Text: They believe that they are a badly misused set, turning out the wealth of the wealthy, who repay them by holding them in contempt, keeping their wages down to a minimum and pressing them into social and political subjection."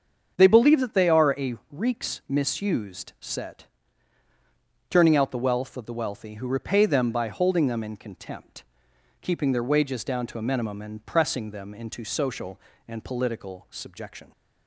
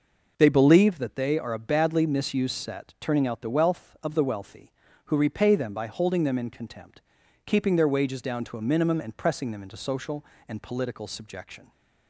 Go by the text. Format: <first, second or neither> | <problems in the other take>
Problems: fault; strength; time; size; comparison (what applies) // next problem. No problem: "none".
second | starts louder than the rest; strong; until 1.3 s; 7 dB // says "reeks" for "badly"; at 1.7 s